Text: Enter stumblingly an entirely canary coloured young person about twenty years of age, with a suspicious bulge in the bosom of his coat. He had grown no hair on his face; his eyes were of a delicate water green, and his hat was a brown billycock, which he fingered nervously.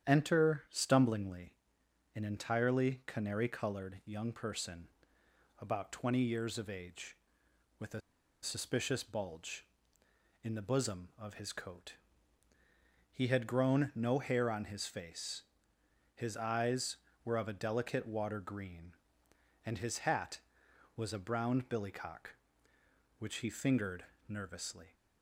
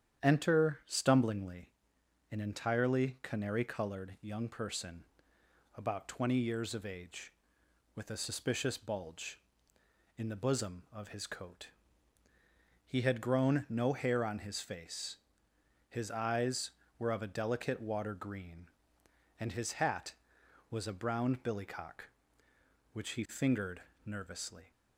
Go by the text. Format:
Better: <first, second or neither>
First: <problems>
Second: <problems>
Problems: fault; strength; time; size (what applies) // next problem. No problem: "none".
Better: second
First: starts louder than the rest; strong; until 1.1 s; 9.5 dB // pauses between "stumblingly" and "an"; noticeable; at 1.5 s; 0.62 s long // pauses between "person" and "about"; noticeable; at 4.8 s; 0.70 s long // pauses between "a" and "suspicious"; at 8.0 s; 0.42 s long // pauses between "fingered" and "nervously"; slight; at 24.0 s; 0.24 s long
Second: starts louder than the rest; strong; until 1.2 s; 9.5 dB // pauses between "stumblingly" and "an"; noticeable; at 1.6 s; 0.62 s long // pauses between "person" and "about"; noticeable; at 5.0 s; 0.70 s long // pauses between "fingered" and "nervously"; slight; at 23.8 s; 0.24 s long